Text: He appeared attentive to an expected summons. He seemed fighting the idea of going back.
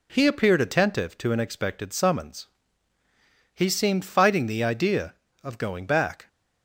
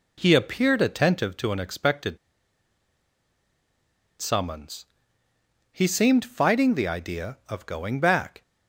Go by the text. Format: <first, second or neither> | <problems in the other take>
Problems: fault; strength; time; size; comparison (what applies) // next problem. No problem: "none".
first | pauses between "expected" and "summons"; strong; at 2.1 s; 2.0 s long